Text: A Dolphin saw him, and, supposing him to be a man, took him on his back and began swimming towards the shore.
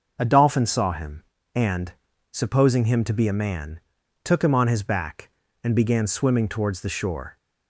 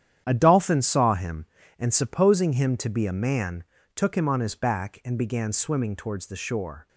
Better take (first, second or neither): first